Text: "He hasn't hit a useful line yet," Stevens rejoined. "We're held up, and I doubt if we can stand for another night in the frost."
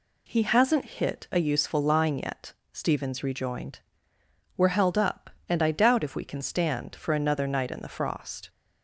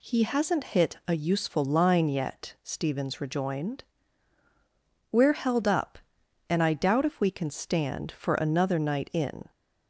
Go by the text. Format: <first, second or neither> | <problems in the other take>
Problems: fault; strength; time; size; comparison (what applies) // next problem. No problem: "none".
first | stops before "the frost"; at 9.5 s